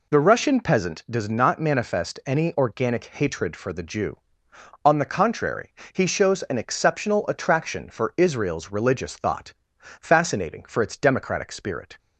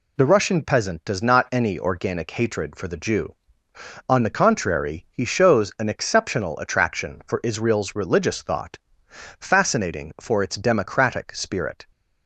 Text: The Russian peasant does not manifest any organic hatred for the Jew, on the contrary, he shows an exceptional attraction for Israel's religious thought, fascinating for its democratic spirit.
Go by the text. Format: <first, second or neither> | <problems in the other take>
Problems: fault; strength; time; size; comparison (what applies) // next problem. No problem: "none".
first | skips "manifest"; at 1.5 s